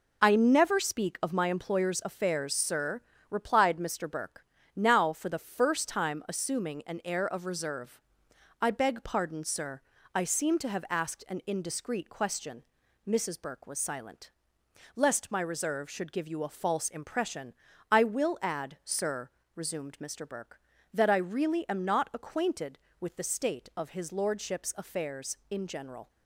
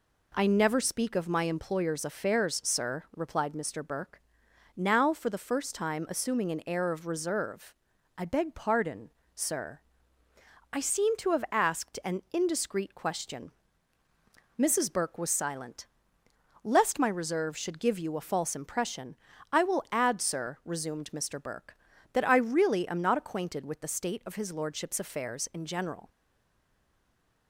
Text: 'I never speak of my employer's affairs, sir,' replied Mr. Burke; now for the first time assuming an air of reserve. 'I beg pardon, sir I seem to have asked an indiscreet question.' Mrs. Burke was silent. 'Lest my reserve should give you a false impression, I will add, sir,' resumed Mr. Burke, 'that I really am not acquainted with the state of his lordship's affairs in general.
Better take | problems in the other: first | pauses between "sir" and "I"; noticeable; at 9.8 s; 0.90 s long; slight in the first // stays silent after the last word; noticeable; from 26.0 s on; 1.4 s long

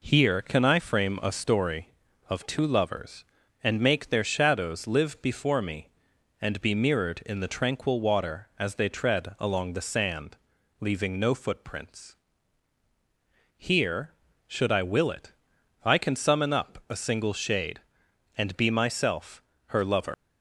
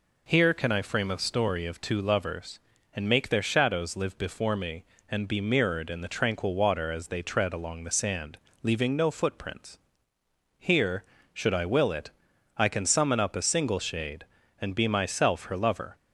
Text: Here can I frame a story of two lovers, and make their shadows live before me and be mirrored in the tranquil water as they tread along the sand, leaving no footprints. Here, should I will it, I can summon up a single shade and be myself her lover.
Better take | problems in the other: second | pauses between "myself" and "her"; slight; at 19.4 s; 0.26 s long // leaves "lover" unfinished; at 20.1 s; 125 ms

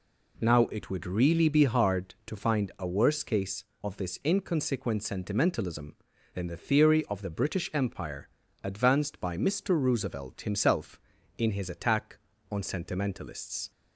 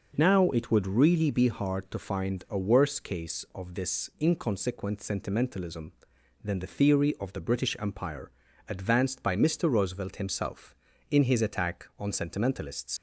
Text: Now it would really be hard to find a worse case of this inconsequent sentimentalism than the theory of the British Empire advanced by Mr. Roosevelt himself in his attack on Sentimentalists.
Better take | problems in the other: first | pauses between "Empire" and "advanced"; at 8.2 s; 0.38 s long; also in the first // leaves "Sentimentalists" unfinished; at 12.9 s; 85 ms

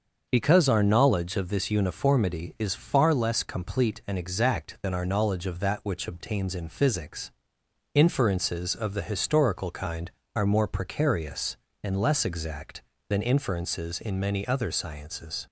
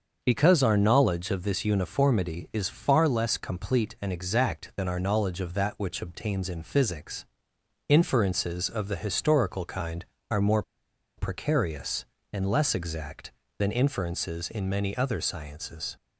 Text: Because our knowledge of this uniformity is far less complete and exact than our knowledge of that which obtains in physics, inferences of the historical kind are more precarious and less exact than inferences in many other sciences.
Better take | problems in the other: first | starts louder than the rest; until 1.2 s; 6.5 dB; also in the first // pauses between "more" and "precarious"; noticeable; at 10.6 s; 0.55 s long

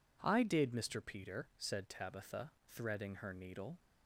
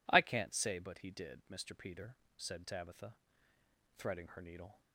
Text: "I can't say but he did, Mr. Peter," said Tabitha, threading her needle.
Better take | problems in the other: second | skips "can't say but he"; at 0.4 s

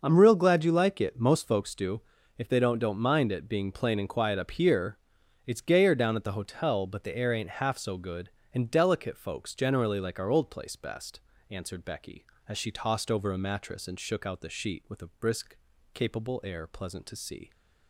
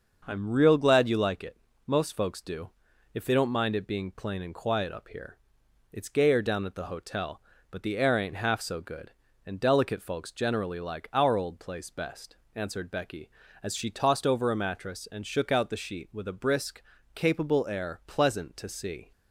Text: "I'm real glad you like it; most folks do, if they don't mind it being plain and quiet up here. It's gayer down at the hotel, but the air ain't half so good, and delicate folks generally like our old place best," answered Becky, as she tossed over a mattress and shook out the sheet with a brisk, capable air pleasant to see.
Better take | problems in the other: second | starts louder than the rest; until 1.0 s; 6 dB; also in the second // says "don't" twice; at 2.7 s

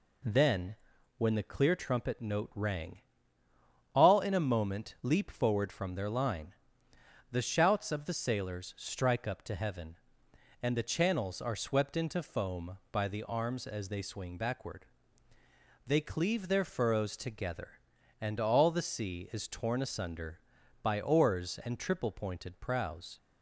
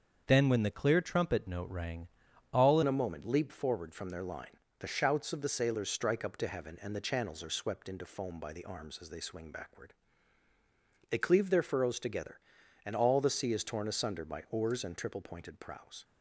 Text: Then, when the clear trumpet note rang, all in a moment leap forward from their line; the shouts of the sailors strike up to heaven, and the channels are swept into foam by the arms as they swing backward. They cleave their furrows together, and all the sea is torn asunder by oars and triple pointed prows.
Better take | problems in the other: first | starts louder than the rest; until 1.2 s; 7 dB // changes voice at "in"; from 2.8 s on; 13.2 s long

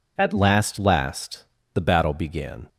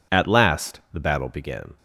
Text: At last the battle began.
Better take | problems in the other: second | says "last" twice; at 0.7 s

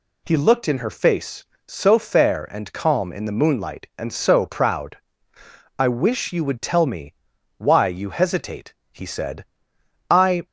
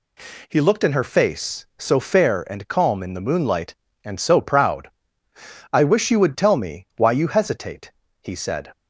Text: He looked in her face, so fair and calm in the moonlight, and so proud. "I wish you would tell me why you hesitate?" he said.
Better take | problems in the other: second | pauses between "me" and "why"; at 7.1 s; 0.44 s long // goes on to say "I"; slight; from 10.0 s on; 0.36 s long

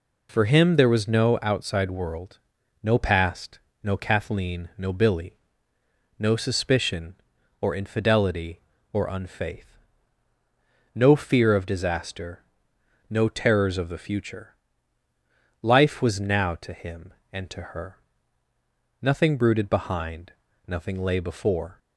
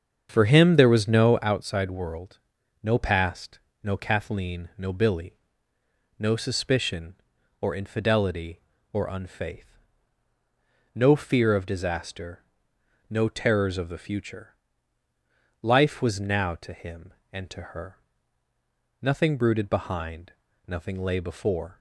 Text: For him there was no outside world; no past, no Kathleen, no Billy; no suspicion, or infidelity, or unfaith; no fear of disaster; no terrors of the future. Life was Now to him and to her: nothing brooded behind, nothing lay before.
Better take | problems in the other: first | starts louder than the rest; strong; until 1.7 s; 7 dB

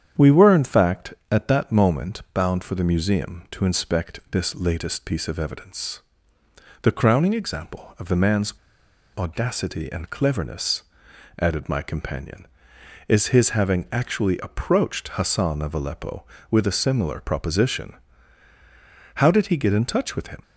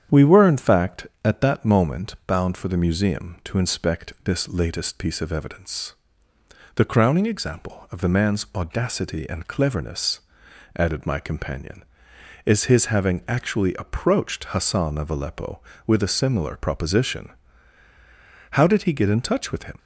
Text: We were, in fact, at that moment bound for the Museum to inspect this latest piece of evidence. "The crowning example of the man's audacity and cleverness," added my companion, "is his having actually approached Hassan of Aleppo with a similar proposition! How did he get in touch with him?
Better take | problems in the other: second | starts louder than the rest; strong; until 1.3 s; 9 dB; strong in the second // pauses between "man's" and "audacity"; noticeable; at 8.5 s; 0.63 s long

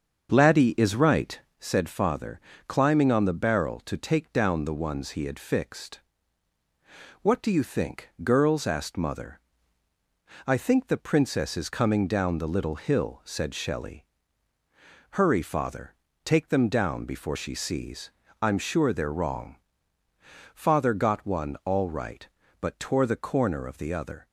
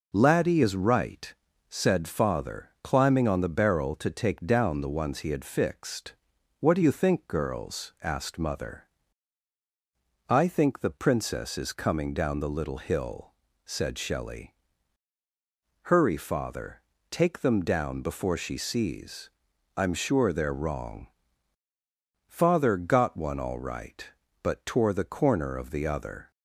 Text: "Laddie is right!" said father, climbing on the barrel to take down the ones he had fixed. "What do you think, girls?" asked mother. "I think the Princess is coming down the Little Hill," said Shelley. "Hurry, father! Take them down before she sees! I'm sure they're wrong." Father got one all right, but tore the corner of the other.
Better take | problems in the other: second | starts louder than the rest; until 1.7 s; 6.5 dB

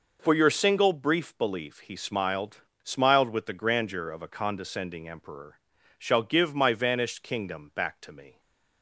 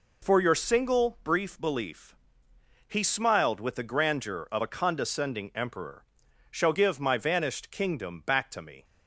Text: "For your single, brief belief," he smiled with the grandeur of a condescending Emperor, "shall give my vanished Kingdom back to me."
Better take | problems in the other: second | says "smiled" twice; at 2.8 s // stays silent after the last word; slight; from 8.3 s on; 0.5 s long

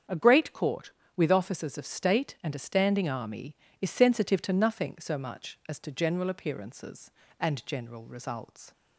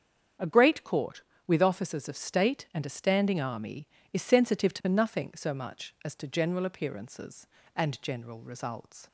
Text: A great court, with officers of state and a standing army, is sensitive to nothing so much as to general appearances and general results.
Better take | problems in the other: neither | starts louder than the rest; strong; the same in both

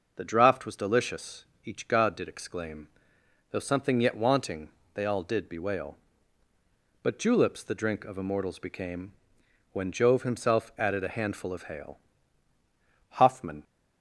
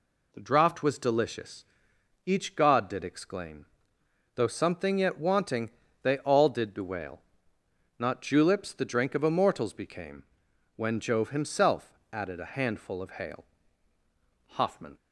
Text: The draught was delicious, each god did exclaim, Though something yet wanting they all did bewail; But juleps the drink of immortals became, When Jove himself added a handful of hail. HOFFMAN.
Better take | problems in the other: first | pauses between "wanting" and "they"; slight; at 5.6 s; 0.34 s long; slight in the first // says "Not" for "But"; at 7.9 s // pauses between "himself" and "added"; slight; at 11.9 s; 0.16 s long

